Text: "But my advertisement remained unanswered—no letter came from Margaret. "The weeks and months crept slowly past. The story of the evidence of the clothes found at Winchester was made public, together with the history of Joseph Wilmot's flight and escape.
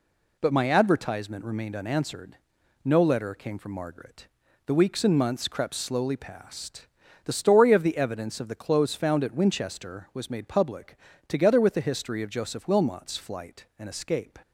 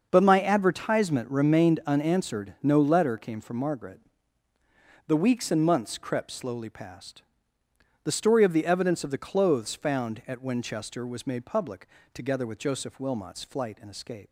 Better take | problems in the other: first | starts louder than the rest; until 1.1 s; 6.5 dB // skips "the history of"; at 12.5 s

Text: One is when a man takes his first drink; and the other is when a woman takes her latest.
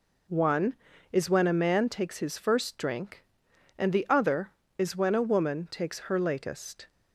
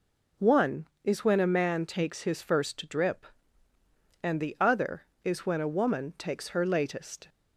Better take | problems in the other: first | says "drip" for "drink"; at 2.8 s

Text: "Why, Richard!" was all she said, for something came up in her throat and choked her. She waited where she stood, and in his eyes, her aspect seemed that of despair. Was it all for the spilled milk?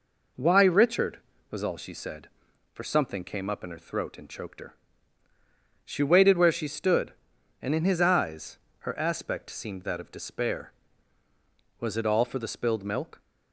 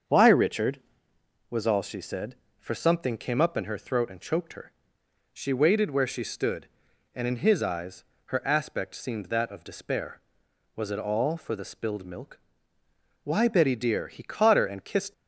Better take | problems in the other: first | starts louder than the rest; until 1.7 s; 7 dB // goes on to say "Why Betty dear He caught her and kissed"; strong; from 13.2 s on; 1.8 s long

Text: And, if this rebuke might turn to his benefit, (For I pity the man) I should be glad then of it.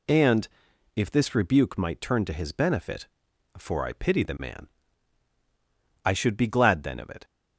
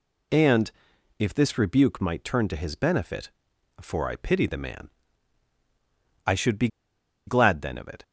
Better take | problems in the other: first | pauses between "be" and "glad"; noticeable; at 6.6 s; 0.59 s long

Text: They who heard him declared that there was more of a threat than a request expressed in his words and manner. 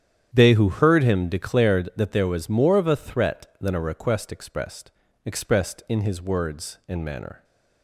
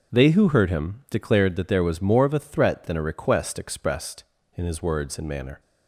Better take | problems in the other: second | starts louder than the rest; strong; until 1.3 s; 9.5 dB // says "expressed" twice; at 5.2 s

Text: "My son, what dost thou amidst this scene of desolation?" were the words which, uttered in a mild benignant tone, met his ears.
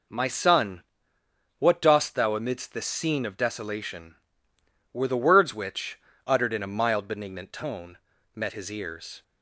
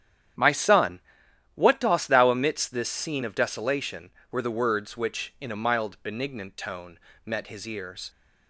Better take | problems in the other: first | starts louder than the rest; strong; until 1.9 s; 10 dB // skips "uttered"; at 5.3 s

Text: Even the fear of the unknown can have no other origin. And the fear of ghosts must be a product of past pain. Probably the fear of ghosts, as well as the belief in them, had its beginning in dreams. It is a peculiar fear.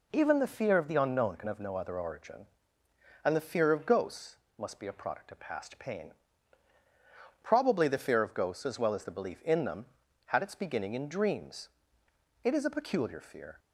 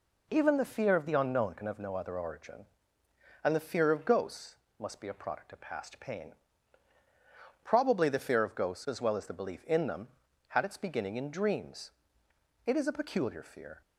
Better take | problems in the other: neither | pauses between "ghosts" and "must"; slight; the same in both

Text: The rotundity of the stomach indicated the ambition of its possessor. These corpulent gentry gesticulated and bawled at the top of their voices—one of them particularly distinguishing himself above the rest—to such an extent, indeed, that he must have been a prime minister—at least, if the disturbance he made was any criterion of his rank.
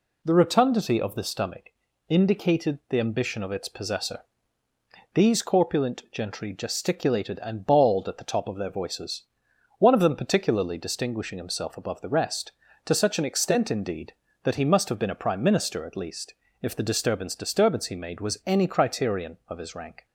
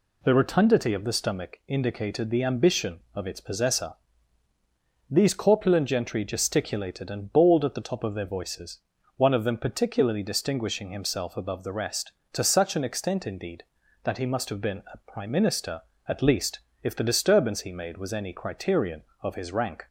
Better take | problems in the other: second | pauses between "stomach" and "indicated"; at 1.6 s; 0.38 s long // says "disturbance" twice; at 17.3 s

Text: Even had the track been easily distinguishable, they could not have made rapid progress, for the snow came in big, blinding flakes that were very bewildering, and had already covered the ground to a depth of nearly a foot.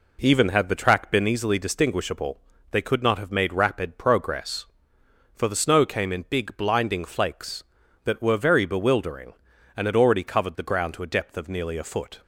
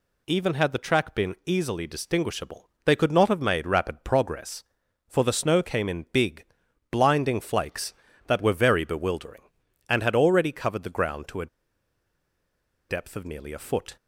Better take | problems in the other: first | pauses between "a" and "depth"; strong; at 11.4 s; 1.4 s long

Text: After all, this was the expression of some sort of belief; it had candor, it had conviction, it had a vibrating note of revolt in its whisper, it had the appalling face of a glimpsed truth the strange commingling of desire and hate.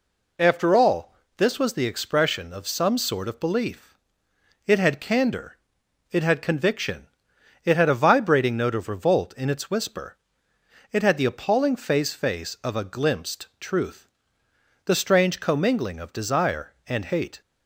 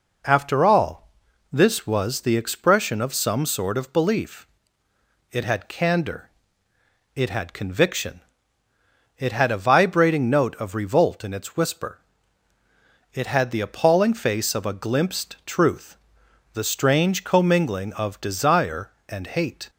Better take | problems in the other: second | says "face" twice; at 12.1 s // pauses between "truth" and "the"; noticeable; at 14.0 s; 0.78 s long; noticeable in the second

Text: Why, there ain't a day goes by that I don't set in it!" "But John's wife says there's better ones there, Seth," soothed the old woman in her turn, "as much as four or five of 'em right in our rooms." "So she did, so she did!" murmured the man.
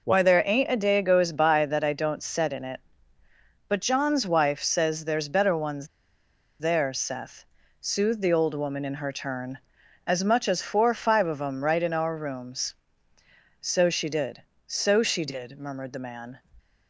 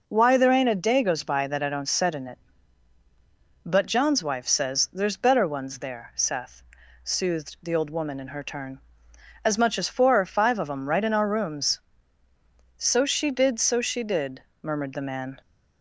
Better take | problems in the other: second | pauses between "ones" and "there"; noticeable; at 5.8 s; 0.72 s long

